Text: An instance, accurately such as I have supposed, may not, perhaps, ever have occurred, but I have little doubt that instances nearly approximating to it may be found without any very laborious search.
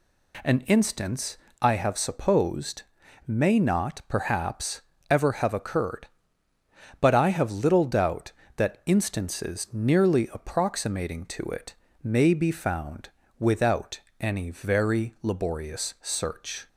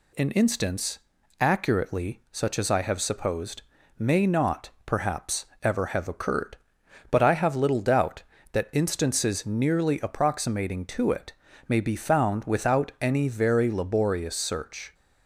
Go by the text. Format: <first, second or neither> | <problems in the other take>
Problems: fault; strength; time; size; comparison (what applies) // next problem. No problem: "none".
second | skips "accurately such as"; at 1.4 s // pauses between "it" and "may"; slight; at 11.7 s; 0.28 s long; slight in the second // pauses between "found" and "without"; slight; at 13.0 s; 0.30 s long // pauses between "without" and "any"; slight; at 13.9 s; 0.20 s long